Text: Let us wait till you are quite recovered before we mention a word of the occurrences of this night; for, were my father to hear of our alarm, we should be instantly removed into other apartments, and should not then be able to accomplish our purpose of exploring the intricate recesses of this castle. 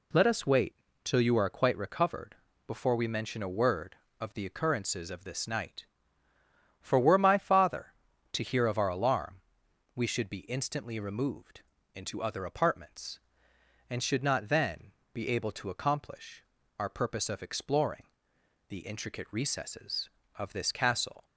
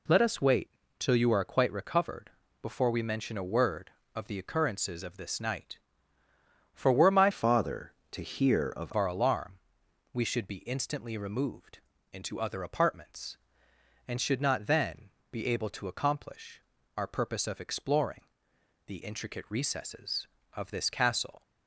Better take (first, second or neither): first